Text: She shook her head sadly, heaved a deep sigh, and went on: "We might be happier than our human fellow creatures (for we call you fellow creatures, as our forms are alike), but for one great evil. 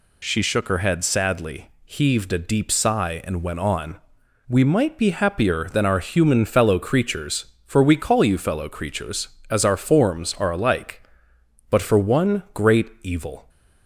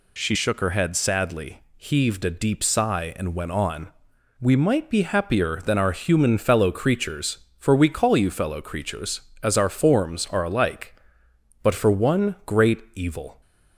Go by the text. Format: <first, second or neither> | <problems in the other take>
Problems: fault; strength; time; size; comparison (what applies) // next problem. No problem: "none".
neither | none